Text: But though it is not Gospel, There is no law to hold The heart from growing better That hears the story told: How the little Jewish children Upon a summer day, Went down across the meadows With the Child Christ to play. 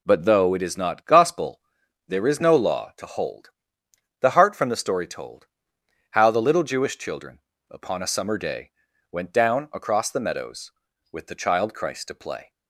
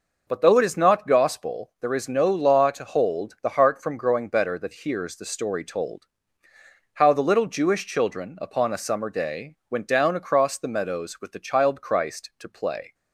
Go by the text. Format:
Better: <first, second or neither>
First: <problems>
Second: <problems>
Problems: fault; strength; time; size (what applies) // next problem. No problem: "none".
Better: second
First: pauses between "hold" and "The"; noticeable; at 3.5 s; 0.68 s long // skips "growing better That hears"; at 4.6 s // pauses between "children" and "Upon"; slight; at 7.3 s; 0.32 s long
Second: none